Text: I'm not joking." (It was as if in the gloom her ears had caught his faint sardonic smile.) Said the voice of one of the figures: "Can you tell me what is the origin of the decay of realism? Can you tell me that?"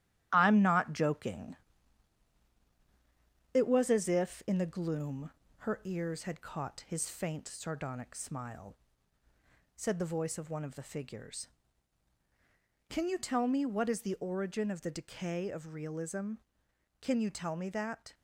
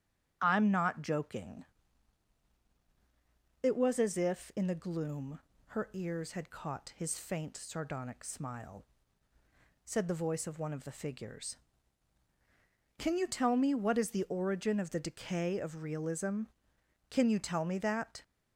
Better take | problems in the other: second | gets quieter; noticeable; throughout; 4.5 dB // starts louder than the rest; strong; until 1.3 s; 13 dB; strong in the second // pauses between "gloom" and "her"; slight; at 5.3 s; 0.32 s long; slight in the second

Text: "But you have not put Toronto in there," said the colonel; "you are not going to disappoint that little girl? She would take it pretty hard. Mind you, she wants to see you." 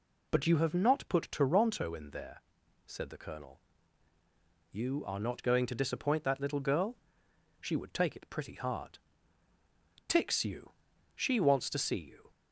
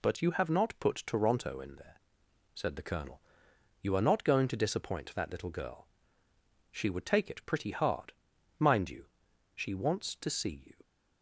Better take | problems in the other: second | says "Tix" for "Mind"; at 10.0 s

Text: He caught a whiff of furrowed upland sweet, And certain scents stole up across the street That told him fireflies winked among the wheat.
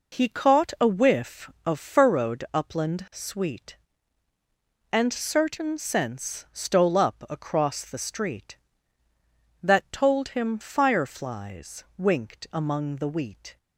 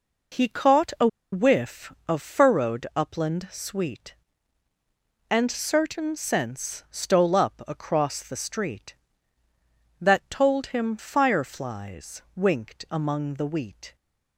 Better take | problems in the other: first | pauses between "a" and "whiff"; slight; at 1.0 s; 0.25 s long // pauses between "fireflies" and "winked"; slight; at 12.2 s; 0.16 s long; slight in the first

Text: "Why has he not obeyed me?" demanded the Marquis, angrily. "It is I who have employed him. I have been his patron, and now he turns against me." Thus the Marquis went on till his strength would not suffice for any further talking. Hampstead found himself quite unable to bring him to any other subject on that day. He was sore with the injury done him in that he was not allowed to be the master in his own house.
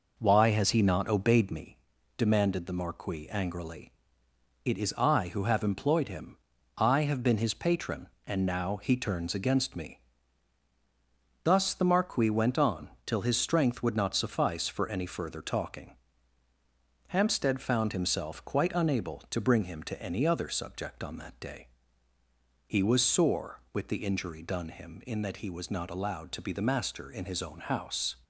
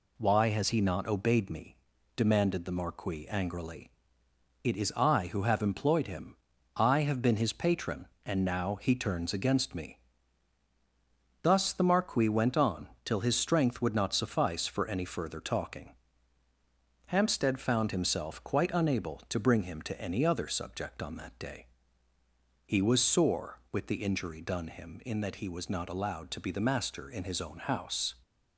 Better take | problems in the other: second | starts louder than the rest; noticeable; until 1.7 s; 5 dB // pauses between "on" and "till"; slight; at 12.8 s; 0.16 s long; slight in the second

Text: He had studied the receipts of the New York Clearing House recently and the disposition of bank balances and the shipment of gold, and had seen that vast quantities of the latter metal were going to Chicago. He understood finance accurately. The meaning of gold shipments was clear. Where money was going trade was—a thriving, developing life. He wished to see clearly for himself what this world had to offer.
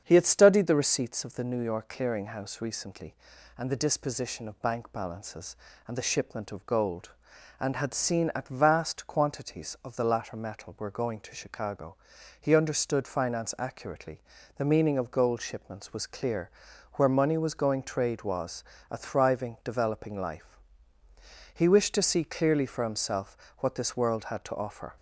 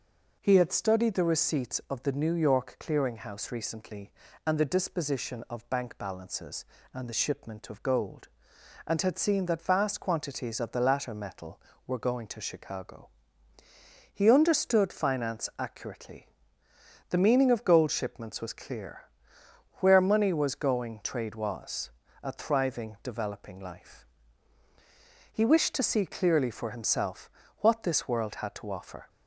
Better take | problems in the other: second | starts louder than the rest; strong; until 1.0 s; 7.5 dB // says "at" for "that"; at 8.3 s // pauses between "himself" and "what"; slight; at 23.3 s; 0.22 s long; slight in the second

